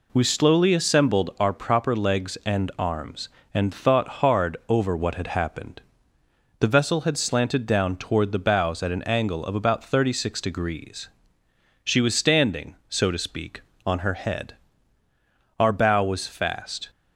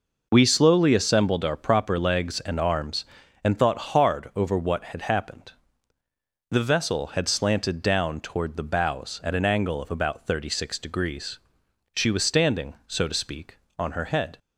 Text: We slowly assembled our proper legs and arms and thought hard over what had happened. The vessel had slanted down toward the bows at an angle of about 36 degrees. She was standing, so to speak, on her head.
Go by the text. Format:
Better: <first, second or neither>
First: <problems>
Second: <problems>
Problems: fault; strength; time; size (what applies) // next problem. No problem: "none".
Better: second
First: goes on to say "Our bow was fast"; noticeable; from 15.5 s on; 1.3 s long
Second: none